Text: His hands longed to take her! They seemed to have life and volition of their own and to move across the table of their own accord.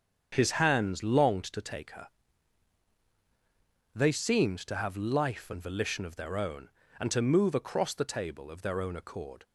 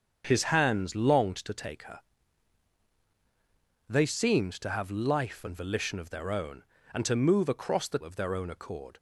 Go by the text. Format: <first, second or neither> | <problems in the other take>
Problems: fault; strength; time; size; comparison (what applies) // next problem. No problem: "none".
first | starts louder than the rest; strong; until 1.2 s; 7.5 dB; strong in the first // skips "table"; at 8.0 s